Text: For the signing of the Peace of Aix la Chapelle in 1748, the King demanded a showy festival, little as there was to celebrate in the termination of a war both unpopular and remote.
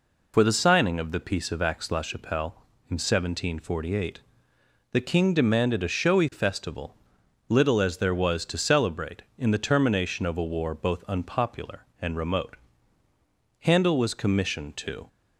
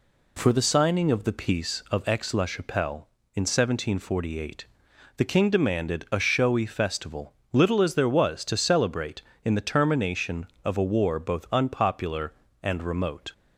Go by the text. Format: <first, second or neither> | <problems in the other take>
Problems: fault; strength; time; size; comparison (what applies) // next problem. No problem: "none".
second | goes on to say "Handel was commissioned to"; from 13.5 s on; 1.4 s long